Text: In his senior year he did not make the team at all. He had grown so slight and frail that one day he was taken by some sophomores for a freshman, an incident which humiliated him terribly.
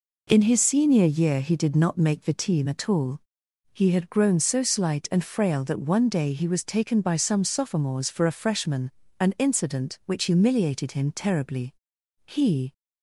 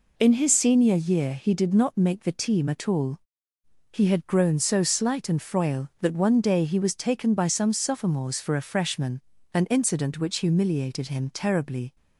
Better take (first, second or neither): second